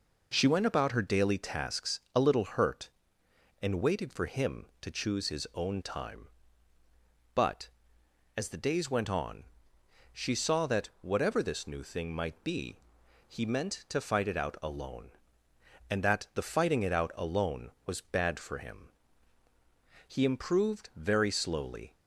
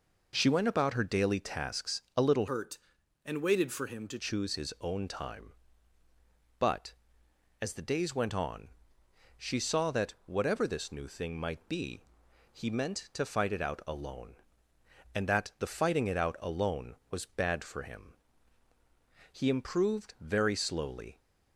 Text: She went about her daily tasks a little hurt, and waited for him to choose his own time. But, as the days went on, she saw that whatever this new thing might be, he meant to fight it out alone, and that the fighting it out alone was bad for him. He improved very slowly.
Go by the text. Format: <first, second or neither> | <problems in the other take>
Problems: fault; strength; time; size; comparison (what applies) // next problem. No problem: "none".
first | changes voice from "hurt" to "to"; from 2.4 to 4.1 s; 1.7 s long